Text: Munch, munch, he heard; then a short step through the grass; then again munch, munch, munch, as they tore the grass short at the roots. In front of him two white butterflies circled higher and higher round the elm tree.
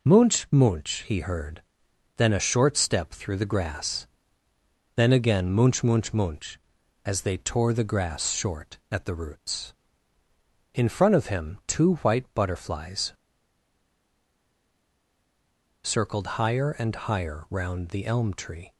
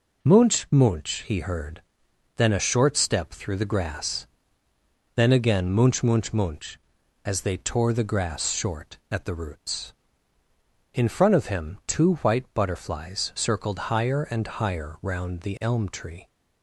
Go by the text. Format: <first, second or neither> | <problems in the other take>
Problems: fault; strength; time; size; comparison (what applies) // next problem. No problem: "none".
second | pauses between "butterflies" and "circled"; strong; at 13.1 s; 2.7 s long